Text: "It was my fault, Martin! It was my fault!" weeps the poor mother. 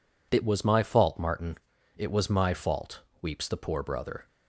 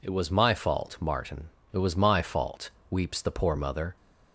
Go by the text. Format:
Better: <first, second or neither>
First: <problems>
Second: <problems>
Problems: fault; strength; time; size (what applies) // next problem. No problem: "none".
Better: second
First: says "brother" for "mother"; at 3.8 s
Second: none